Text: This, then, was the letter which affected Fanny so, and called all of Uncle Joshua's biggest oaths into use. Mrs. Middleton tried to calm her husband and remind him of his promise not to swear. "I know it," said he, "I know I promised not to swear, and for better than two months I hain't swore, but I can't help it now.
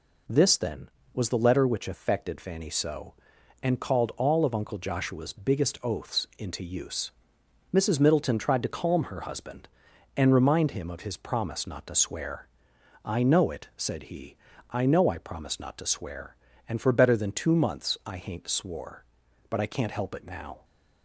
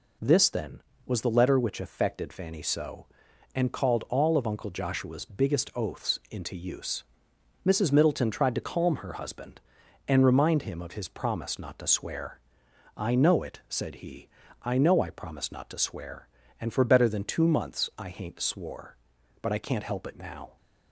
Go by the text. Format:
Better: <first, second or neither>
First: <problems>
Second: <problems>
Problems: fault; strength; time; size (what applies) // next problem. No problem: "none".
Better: neither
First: none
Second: none